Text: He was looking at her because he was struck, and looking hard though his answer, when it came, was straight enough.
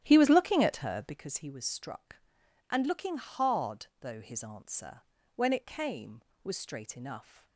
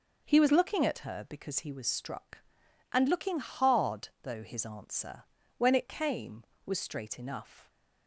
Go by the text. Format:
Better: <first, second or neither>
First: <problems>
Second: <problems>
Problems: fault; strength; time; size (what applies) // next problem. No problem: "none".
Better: second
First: starts louder than the rest; strong; until 1.2 s; 11.5 dB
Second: none